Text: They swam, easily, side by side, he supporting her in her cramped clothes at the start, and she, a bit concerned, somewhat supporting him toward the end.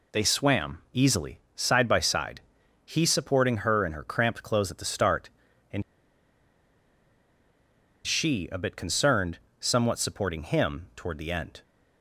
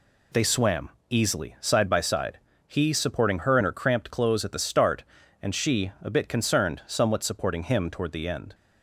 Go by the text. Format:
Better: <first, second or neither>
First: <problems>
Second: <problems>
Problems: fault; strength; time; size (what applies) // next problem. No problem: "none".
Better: second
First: pauses between "and" and "she"; strong; at 5.8 s; 2.2 s long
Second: none